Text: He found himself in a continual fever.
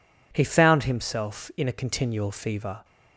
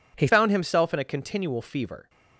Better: first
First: none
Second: changes voice at "found"; from 0.2 s on; 1.8 s long

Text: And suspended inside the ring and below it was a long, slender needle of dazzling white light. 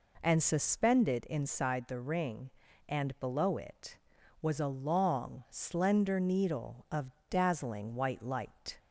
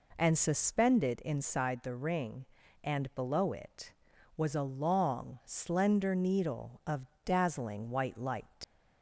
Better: first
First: pauses between "of" and "dazzling"; slight; at 7.1 s; 0.20 s long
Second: pauses between "of" and "dazzling"; slight; at 7.0 s; 0.20 s long // leaves "light" unfinished; at 8.6 s; 90 ms

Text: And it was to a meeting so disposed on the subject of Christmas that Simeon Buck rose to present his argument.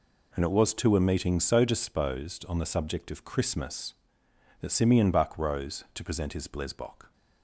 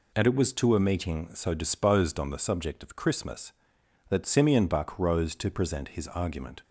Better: second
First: says "blesbok" for "argument"; at 6.4 s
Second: none

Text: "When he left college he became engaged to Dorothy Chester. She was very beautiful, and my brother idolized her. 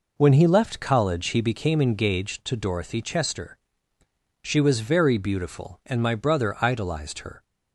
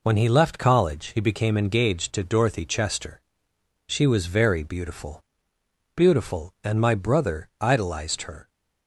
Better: first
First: none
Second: says "beautiful" twice; at 5.9 s

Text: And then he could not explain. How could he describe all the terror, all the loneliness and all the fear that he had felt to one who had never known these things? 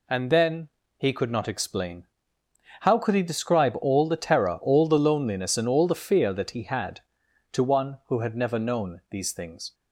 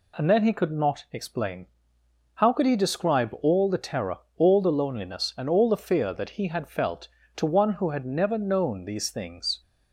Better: second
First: pauses between "then" and "he"; slight; at 0.6 s; 0.28 s long // skips "felt"; at 7.2 s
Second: none

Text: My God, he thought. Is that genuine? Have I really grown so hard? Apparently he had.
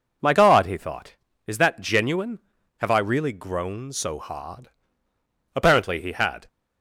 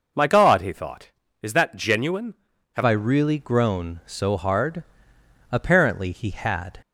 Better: first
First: none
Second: changes voice at "I"; from 2.8 s on; 4.0 s long

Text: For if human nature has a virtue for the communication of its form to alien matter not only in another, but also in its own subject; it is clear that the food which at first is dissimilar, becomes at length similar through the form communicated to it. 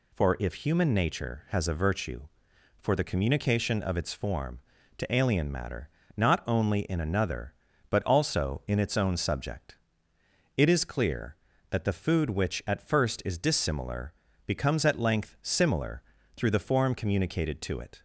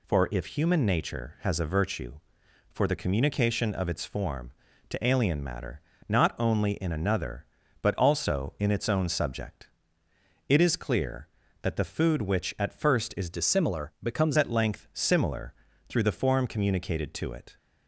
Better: first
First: pauses between "matter" and "not"; slight; at 5.8 s; 0.26 s long // pauses between "similar" and "through"; slight; at 16.0 s; 0.32 s long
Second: pauses between "matter" and "not"; slight; at 5.8 s; 0.26 s long // changes voice from "dissimilar" to "becomes"; from 13.3 to 14.3 s; 1.0 s long // pauses between "similar" and "through"; slight; at 15.5 s; 0.34 s long

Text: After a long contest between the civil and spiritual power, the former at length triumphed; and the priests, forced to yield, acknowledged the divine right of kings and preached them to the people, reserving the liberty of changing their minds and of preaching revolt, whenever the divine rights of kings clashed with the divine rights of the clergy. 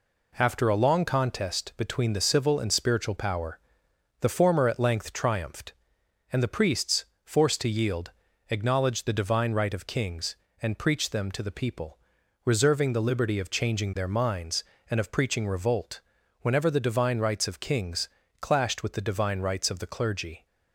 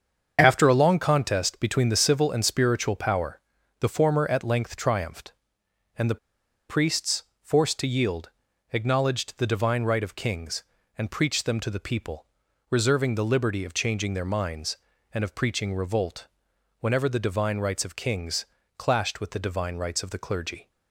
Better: first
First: pauses between "kings" and "clashed"; slight; at 18.0 s; 0.32 s long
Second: starts louder than the rest; until 1.4 s; 7 dB // pauses between "the" and "priests"; noticeable; at 6.1 s; 0.52 s long // pauses between "kings" and "clashed"; slight; at 18.4 s; 0.30 s long

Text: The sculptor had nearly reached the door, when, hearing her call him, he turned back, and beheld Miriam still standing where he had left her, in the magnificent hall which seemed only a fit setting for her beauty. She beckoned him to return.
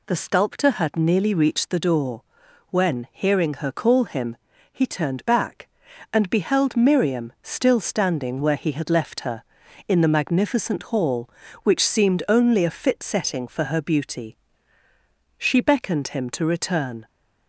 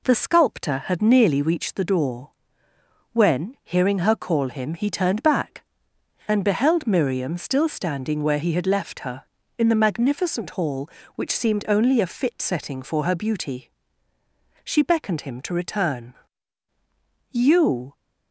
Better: first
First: none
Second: goes on to say "You"; noticeable; from 17.3 s on; 0.62 s long

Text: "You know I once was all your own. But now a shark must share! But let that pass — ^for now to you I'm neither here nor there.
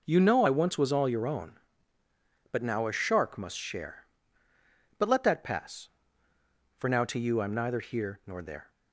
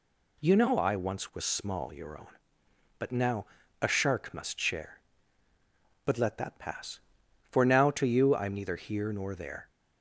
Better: first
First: none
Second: says "small" for "all"; at 1.4 s // pauses between "now" and "a"; at 3.4 s; 0.38 s long

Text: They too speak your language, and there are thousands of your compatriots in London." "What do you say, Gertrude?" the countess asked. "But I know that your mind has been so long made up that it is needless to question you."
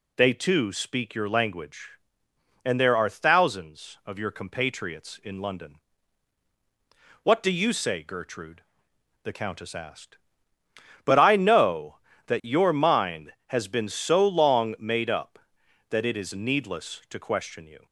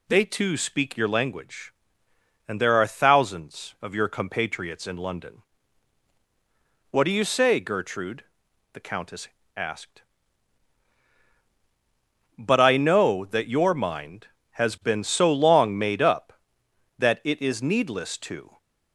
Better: first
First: none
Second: pauses between "countess" and "asked"; slight; at 9.2 s; 0.30 s long // stops before "question you"; at 18.5 s

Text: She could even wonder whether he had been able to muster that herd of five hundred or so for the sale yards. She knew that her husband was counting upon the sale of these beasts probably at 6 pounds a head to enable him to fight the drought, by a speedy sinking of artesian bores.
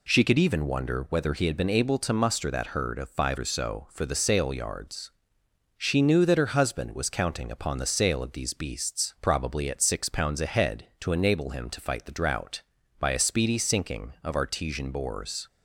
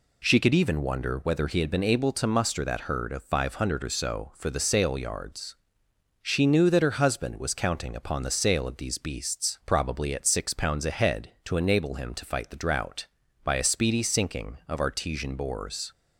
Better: second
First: skips "hundred"; at 3.3 s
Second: none

